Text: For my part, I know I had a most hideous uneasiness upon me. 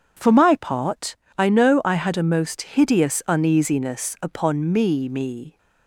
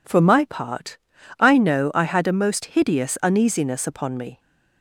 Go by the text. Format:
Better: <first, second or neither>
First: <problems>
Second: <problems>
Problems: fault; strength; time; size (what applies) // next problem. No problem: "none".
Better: second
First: starts louder than the rest; strong; until 1.4 s; 7.5 dB // says "me" twice; at 5.0 s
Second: none